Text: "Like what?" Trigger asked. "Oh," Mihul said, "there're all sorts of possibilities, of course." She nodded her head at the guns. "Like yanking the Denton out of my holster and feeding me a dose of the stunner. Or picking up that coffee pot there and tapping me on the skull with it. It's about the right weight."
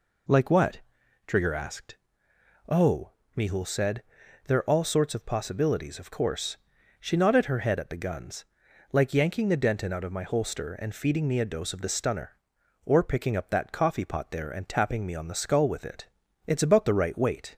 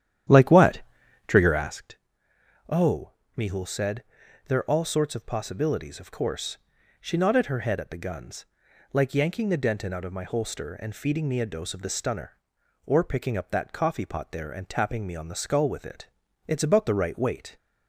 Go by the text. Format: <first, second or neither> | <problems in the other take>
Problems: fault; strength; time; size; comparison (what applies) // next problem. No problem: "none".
first | starts louder than the rest; strong; until 1.8 s; 10.5 dB